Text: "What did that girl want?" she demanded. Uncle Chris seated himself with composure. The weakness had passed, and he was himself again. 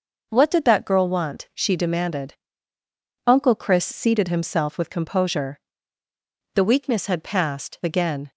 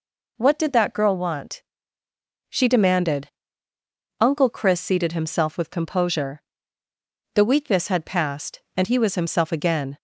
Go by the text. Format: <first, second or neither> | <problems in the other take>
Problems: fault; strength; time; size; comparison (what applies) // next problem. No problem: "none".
second | skips "and he was himself"; at 7.8 s